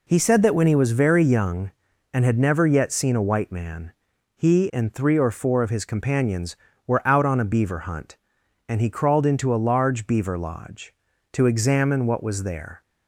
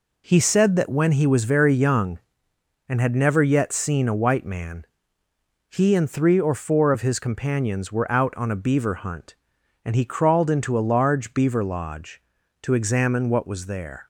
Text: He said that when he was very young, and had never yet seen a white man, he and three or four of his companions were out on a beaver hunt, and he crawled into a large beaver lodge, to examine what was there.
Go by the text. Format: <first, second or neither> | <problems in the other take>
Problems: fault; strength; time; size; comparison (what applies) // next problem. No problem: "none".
neither | none